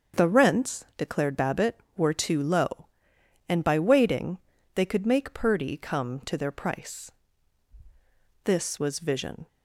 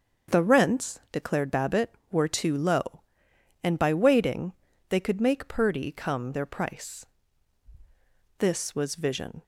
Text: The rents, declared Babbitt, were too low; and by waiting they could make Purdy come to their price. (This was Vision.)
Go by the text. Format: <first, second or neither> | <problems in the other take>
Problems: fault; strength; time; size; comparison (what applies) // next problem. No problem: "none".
first | starts louder than the rest; until 1.4 s; 6.5 dB; also in the first // pauses between "waiting" and "they"; slight; at 4.5 s; 0.36 s long; slight in the first // skips "to"; at 6.3 s